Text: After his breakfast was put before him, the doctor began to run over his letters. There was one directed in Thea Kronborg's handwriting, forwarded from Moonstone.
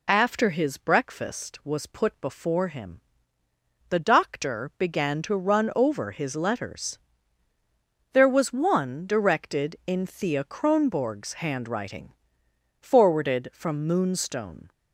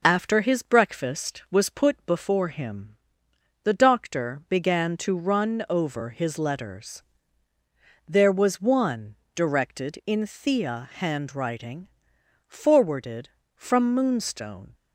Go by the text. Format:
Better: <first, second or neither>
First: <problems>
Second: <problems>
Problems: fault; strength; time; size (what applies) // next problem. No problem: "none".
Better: first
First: none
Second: pauses between "one" and "directed"; slight; at 9.1 s; 0.22 s long // skips "Kronborg's"; at 10.9 s